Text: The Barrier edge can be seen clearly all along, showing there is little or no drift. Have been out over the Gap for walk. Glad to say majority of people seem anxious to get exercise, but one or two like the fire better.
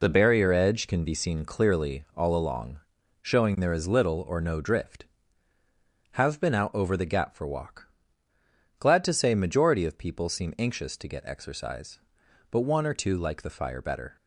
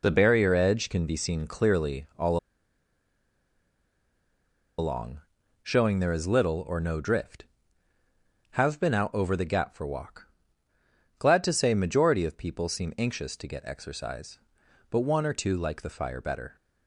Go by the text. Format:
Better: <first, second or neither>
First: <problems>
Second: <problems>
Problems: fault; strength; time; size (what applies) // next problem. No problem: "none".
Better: first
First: none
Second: pauses between "all" and "along"; strong; at 2.3 s; 2.4 s long